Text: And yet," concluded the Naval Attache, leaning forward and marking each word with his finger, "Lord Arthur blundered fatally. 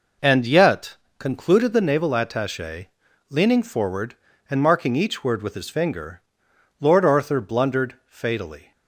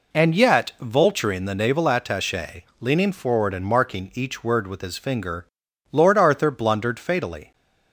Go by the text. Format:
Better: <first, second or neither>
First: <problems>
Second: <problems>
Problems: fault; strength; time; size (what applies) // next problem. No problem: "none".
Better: first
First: none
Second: says "vulturing" for "concluded"; at 0.8 s